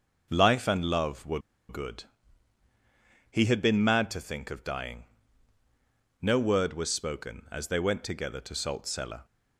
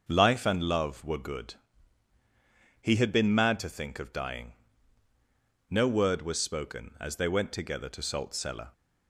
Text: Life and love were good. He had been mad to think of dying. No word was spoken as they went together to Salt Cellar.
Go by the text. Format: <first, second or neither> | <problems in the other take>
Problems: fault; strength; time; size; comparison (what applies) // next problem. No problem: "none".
second | starts louder than the rest; until 1.3 s; 6 dB; also in the second // pauses between "were" and "good"; slight; at 1.3 s; 0.29 s long